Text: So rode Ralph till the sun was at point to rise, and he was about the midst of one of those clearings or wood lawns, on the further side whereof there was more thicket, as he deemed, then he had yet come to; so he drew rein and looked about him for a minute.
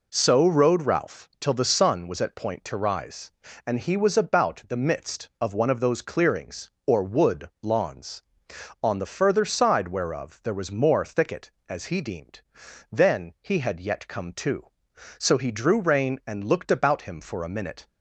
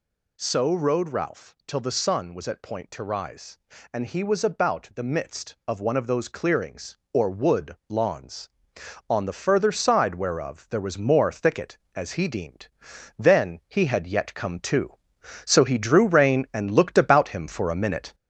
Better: first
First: none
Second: gets louder; throughout; 4 dB

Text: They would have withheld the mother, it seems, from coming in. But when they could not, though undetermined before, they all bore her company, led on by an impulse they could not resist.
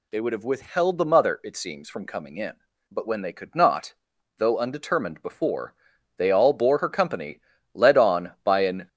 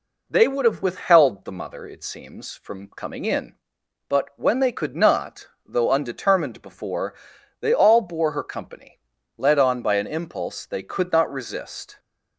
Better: second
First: stops before "impulse they could not resist"; at 8.8 s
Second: none

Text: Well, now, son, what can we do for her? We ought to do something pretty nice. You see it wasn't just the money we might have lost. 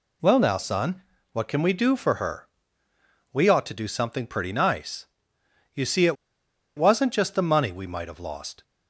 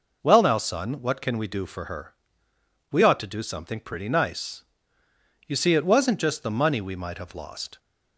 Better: second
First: pauses between "it" and "wasn't"; noticeable; at 6.1 s; 0.61 s long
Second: none

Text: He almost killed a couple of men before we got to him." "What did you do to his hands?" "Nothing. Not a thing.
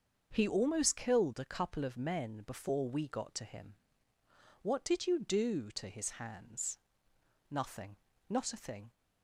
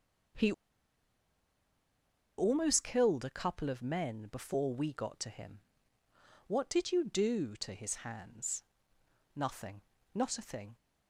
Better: first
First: starts louder than the rest; until 1.3 s; 6.5 dB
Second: starts louder than the rest; until 3.2 s; 6.5 dB // pauses between "He" and "almost"; strong; at 0.5 s; 1.8 s long

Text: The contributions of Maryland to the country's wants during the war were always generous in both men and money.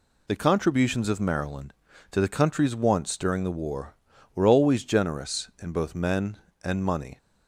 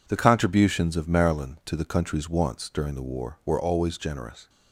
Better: first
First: none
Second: stops before "in both men and money"; at 4.4 s

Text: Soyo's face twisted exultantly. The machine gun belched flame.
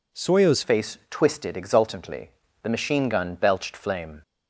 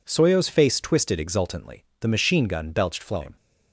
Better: second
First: changes voice at "face"; from 0.6 s on; 3.6 s long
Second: none

